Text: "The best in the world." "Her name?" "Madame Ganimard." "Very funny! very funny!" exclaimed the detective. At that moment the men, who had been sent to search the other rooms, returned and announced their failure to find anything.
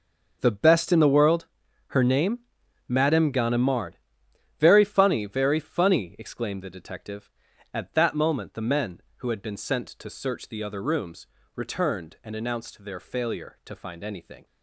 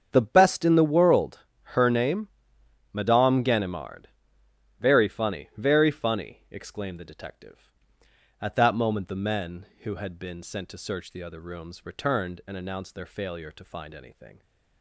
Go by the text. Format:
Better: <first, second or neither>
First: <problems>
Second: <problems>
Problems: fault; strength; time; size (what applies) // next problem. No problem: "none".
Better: neither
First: starts louder than the rest; until 1.4 s; 6 dB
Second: starts louder than the rest; strong; until 1.1 s; 7.5 dB